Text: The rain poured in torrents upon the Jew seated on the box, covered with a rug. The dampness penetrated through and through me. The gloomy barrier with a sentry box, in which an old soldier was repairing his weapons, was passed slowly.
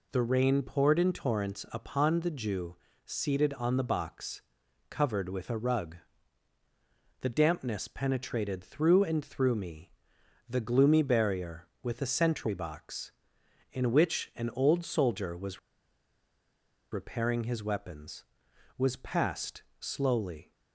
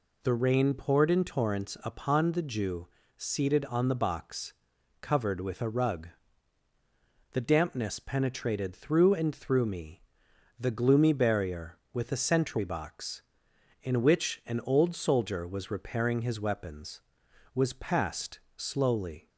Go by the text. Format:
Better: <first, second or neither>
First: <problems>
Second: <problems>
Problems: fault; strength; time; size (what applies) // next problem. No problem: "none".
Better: second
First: pauses between "Jew" and "seated"; slight; at 2.7 s; 0.28 s long // pauses between "was" and "repairing"; strong; at 15.5 s; 1.3 s long // pauses between "passed" and "slowly"; slight; at 19.6 s; 0.16 s long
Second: pauses between "Jew" and "seated"; slight; at 2.8 s; 0.28 s long // pauses between "passed" and "slowly"; slight; at 18.4 s; 0.16 s long